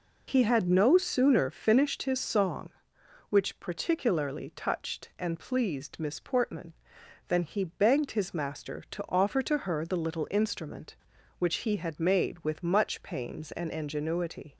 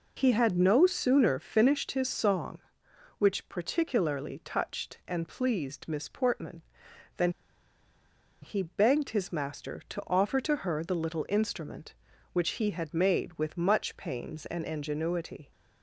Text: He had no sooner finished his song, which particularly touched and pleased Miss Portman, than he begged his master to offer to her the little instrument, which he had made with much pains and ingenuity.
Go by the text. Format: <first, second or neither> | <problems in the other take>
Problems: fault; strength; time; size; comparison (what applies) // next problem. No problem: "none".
first | pauses between "than" and "he"; at 7.2 s; 1.1 s long